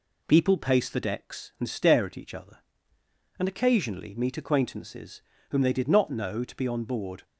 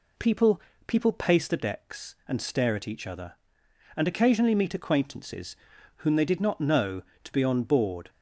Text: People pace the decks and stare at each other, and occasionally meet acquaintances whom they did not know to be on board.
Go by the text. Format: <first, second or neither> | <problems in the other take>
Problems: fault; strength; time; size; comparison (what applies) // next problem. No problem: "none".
first | says "People" twice; at 0.8 s // pauses between "acquaintances" and "whom"; at 5.5 s; 0.42 s long; slight in the first